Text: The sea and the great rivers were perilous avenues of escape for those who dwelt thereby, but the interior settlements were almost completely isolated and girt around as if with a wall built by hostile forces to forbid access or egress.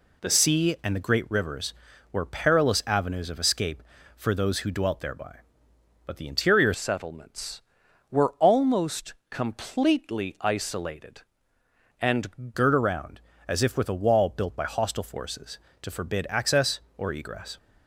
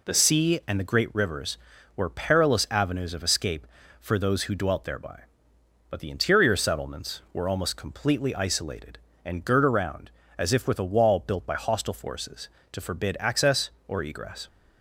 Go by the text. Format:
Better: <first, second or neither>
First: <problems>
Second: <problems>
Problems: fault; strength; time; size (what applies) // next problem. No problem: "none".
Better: second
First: changes voice from "settlements" to "and"; from 6.7 to 12.5 s; 5.8 s long // pauses between "almost" and "completely"; slight; at 9.1 s; 0.16 s long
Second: none